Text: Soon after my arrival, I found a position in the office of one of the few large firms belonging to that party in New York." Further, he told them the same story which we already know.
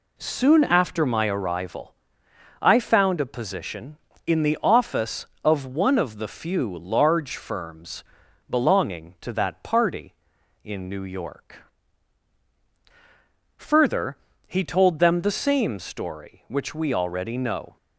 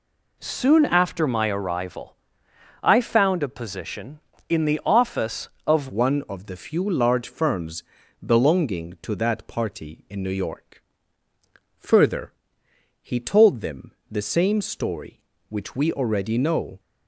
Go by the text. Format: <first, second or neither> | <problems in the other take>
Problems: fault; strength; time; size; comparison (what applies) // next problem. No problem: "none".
first | changes voice at "one"; from 5.8 s on; 10.9 s long // pauses between "firms" and "belonging"; at 7.8 s; 0.42 s long; noticeable in the first // pauses between "them" and "the"; slight; at 13.9 s; 0.18 s long